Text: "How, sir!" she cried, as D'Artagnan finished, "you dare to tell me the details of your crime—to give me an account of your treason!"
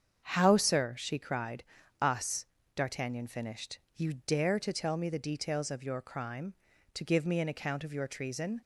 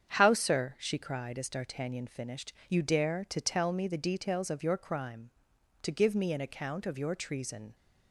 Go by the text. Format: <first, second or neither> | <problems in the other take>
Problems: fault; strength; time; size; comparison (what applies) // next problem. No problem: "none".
second | starts louder than the rest; strong; until 1.3 s; 7.5 dB; strong in the second // says "us" for "as"; at 1.9 s